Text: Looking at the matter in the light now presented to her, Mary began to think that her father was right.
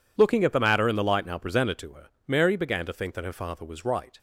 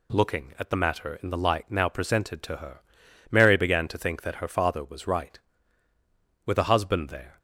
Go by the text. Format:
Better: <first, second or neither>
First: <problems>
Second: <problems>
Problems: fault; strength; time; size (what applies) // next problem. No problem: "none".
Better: first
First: none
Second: goes on to say "With a husband there"; noticeable; from 6.4 s on; 0.94 s long